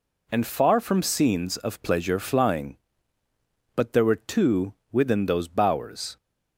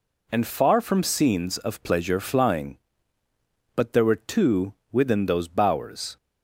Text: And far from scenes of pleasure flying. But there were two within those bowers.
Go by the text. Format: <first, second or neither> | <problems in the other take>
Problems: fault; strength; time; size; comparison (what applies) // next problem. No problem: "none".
neither | pauses between "two" and "within"; slight; the same in both